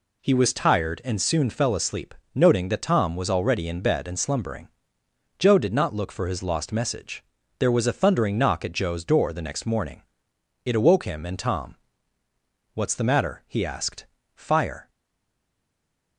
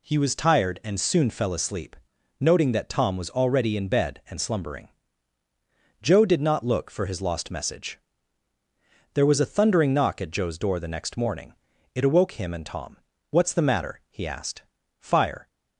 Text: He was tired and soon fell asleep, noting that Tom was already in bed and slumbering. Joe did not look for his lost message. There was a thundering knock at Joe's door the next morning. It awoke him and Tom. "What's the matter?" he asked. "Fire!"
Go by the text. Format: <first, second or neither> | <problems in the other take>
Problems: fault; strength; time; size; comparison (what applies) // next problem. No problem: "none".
second | stays silent after the last word; noticeable; from 14.8 s on; 1.3 s long